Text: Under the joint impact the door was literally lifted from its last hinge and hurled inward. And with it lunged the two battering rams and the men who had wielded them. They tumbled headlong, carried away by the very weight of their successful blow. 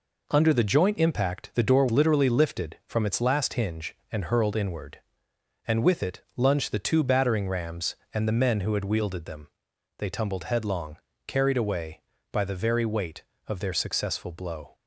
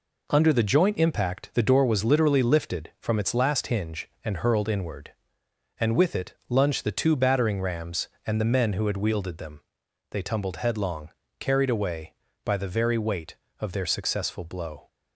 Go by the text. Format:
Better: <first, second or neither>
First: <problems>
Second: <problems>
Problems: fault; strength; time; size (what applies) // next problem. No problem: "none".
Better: second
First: skips "was"; at 1.8 s // pauses between "it" and "lunged"; slight; at 6.2 s; 0.16 s long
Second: pauses between "it" and "lunged"; slight; at 6.3 s; 0.16 s long